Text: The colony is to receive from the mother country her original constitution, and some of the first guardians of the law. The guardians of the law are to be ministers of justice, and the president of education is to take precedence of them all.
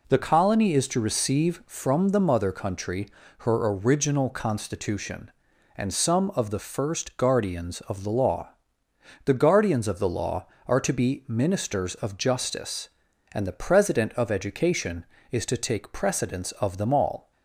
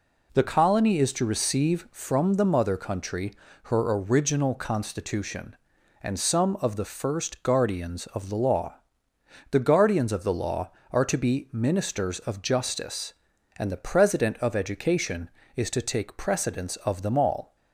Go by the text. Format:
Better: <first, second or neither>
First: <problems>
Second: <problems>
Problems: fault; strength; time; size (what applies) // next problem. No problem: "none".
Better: neither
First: pauses between "country" and "her"; slight; at 3.0 s; 0.30 s long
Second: pauses between "country" and "her"; slight; at 3.3 s; 0.30 s long